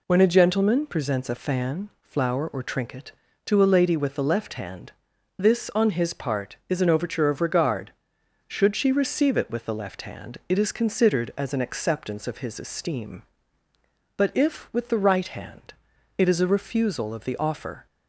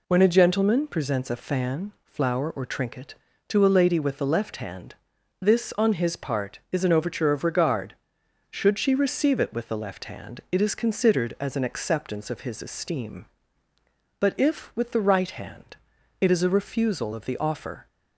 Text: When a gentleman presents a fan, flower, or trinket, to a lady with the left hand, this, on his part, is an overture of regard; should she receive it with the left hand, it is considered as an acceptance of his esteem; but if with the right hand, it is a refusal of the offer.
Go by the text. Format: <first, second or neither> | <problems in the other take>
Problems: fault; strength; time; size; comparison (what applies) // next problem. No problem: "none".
neither | none